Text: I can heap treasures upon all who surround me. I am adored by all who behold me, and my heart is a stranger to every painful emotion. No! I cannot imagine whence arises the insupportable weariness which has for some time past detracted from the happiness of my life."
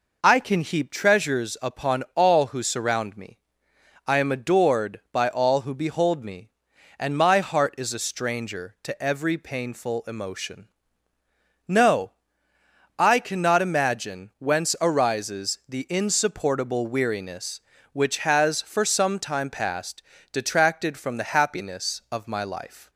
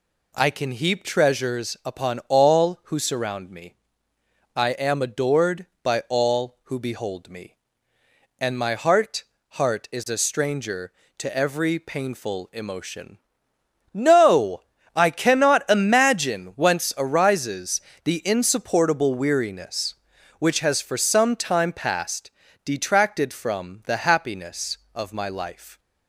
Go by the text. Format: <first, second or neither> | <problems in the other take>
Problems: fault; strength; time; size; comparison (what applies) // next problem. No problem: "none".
first | says "heart" twice; at 9.5 s // pauses between "arises" and "the"; slight; at 17.7 s; 0.24 s long // pauses between "past" and "detracted"; slight; at 22.3 s; 0.34 s long; slight in the first